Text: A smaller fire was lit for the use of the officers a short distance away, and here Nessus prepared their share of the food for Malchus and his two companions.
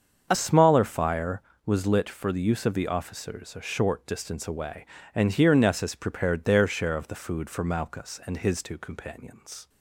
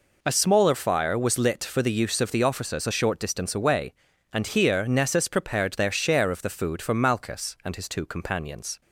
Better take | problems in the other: second | starts louder than the rest; until 1.3 s; 7 dB // changes voice at "smaller"; from 0.3 s on; 9.3 s long

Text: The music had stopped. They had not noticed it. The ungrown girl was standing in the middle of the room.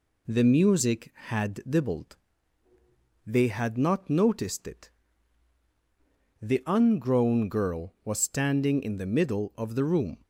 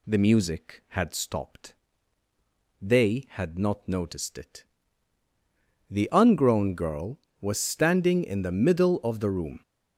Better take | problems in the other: second | says "dibbled" for "stopped"; at 1.7 s

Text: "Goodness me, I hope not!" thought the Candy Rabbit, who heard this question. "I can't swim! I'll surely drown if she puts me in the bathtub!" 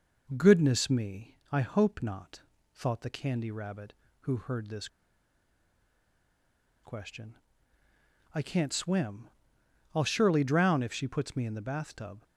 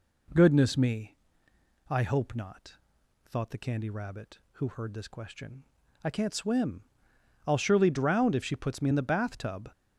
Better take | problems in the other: second | pauses between "this" and "question"; strong; at 4.8 s; 1.9 s long

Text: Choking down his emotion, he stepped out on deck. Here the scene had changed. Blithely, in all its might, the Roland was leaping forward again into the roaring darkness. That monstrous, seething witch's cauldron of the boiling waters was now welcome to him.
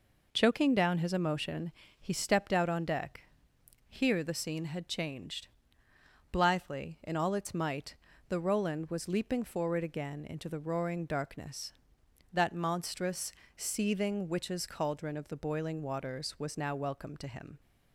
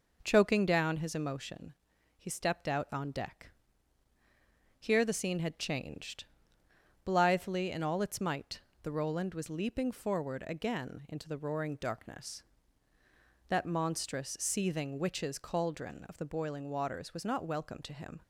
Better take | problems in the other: first | says "not" for "now"; at 17.2 s

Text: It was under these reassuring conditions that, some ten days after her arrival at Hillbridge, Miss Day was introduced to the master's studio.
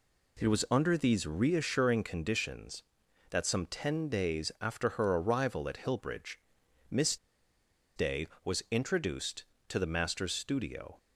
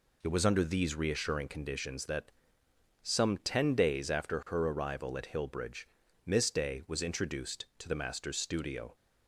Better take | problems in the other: second | pauses between "Miss" and "Day"; noticeable; at 7.1 s; 0.80 s long

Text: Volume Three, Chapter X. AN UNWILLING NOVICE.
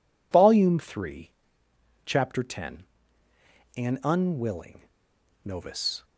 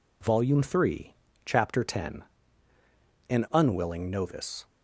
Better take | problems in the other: second | pauses between "UNWILLING" and "NOVICE"; noticeable; at 4.8 s; 0.63 s long

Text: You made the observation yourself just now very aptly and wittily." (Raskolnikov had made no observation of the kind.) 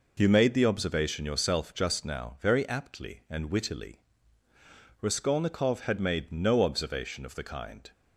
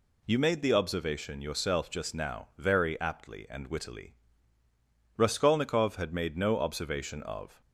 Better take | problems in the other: first | stops before "the kind"; at 7.6 s

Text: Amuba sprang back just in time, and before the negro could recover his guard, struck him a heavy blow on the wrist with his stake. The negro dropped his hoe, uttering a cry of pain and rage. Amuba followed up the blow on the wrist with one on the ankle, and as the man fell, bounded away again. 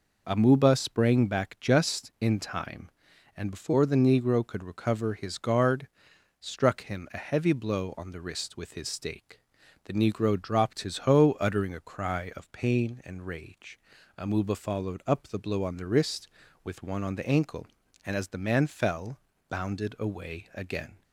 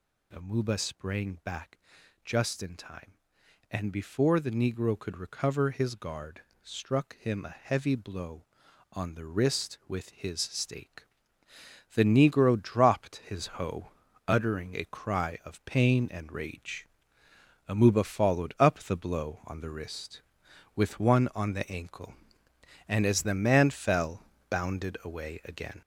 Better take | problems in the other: first | gets louder; noticeable; throughout; 5.5 dB // pauses between "back" and "just"; noticeable; at 1.7 s; 0.46 s long

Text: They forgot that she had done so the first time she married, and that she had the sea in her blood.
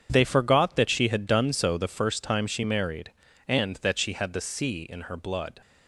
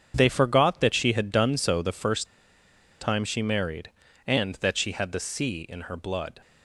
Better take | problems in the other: first | starts louder than the rest; strong; until 1.1 s; 7.5 dB; strong in the first // pauses between "first" and "time"; noticeable; at 2.2 s; 0.74 s long

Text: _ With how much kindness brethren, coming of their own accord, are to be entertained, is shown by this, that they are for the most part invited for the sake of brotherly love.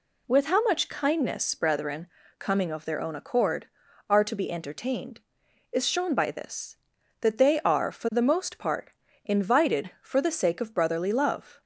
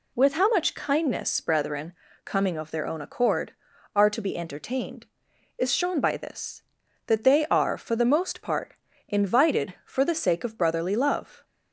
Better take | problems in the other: neither | pauses between "part" and "invited"; slight; the same in both

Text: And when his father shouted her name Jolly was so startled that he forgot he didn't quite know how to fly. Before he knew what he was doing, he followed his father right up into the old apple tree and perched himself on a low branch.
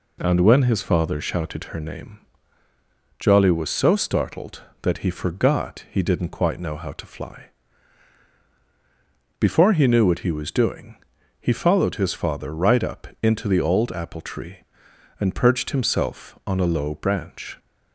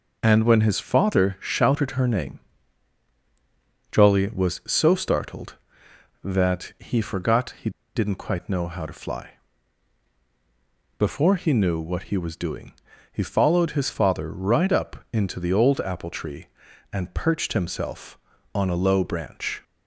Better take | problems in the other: first | pauses between "name" and "Jolly"; strong; at 2.4 s; 1.5 s long; also in the first // pauses between "he" and "didn't"; slight; at 7.7 s; 0.24 s long

